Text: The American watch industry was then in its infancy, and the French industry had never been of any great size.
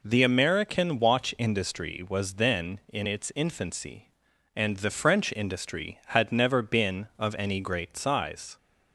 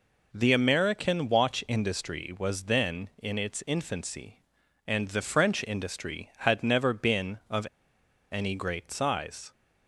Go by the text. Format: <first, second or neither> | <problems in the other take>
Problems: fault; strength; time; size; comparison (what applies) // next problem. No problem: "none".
first | pauses between "of" and "any"; noticeable; at 7.6 s; 0.66 s long